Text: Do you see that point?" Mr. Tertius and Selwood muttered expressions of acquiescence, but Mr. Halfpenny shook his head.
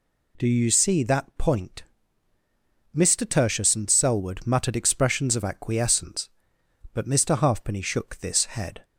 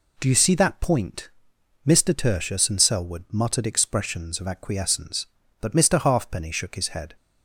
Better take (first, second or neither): second